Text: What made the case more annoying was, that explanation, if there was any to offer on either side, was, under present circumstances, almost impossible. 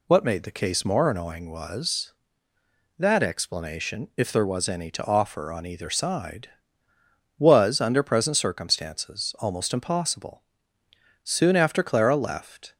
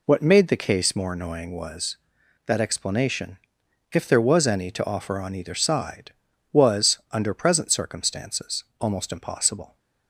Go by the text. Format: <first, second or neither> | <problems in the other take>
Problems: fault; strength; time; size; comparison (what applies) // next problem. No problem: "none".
second | goes on to say "Soon after Clara left"; from 11.2 s on; 1.5 s long